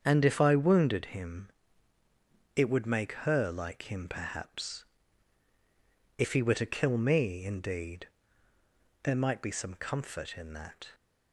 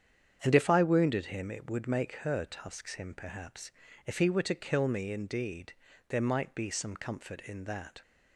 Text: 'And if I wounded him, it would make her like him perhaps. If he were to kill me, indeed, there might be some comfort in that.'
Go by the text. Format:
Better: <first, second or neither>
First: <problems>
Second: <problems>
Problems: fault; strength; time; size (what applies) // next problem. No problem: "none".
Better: first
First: starts louder than the rest; strong; until 1.0 s; 7.5 dB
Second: starts louder than the rest; strong; until 1.4 s; 8 dB // says "tusks" for "like"; at 2.4 s